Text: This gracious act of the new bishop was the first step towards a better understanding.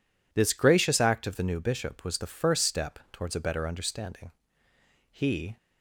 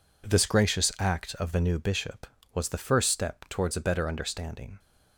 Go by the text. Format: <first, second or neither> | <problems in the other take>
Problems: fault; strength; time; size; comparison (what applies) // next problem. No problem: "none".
second | goes on to say "He"; slight; from 5.1 s on; 0.46 s long